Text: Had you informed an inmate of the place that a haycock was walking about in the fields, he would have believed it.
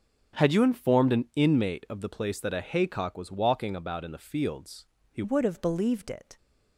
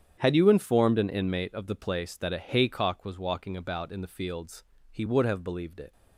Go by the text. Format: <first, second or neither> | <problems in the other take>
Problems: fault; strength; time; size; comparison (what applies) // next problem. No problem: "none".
second | starts louder than the rest; strong; until 1.4 s; 8 dB; strong in the second // changes voice at "would"; from 5.2 s on; 1.1 s long